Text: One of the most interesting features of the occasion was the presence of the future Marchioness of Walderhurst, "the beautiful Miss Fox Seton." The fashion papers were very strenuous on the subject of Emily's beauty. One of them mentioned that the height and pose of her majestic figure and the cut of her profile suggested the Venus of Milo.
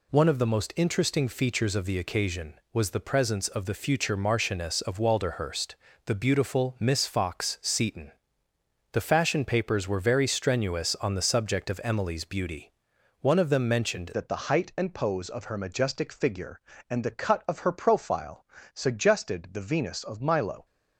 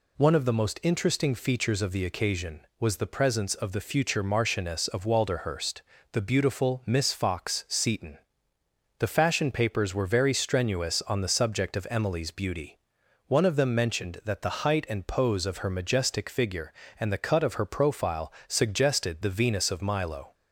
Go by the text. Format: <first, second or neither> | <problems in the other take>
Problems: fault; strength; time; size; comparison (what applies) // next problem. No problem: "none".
second | changes voice at "that"; from 14.1 s on; 6.5 s long // pauses between "profile" and "suggested"; slight; at 18.4 s; 0.30 s long; slight in the second